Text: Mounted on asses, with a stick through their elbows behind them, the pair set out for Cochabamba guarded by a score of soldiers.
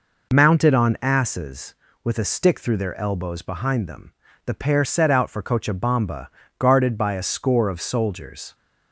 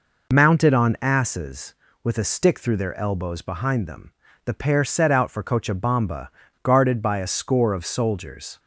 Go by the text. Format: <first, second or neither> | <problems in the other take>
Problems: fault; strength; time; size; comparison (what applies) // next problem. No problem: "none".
neither | pauses between "Cochabamba" and "guarded"; slight; the same in both